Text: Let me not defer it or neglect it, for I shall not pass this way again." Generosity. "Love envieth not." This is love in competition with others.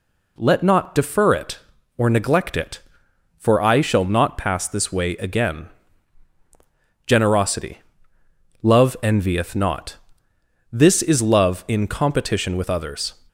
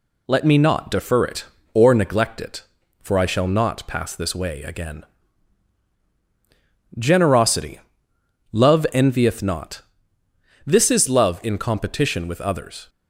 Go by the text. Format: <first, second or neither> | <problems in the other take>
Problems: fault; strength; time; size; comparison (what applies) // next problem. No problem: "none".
second | skips "me"; at 0.6 s